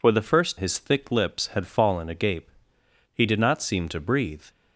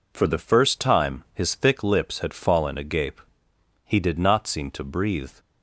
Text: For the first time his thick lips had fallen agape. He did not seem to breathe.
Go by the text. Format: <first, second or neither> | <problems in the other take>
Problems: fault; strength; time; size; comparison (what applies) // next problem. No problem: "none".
second | skips "time"; at 0.5 s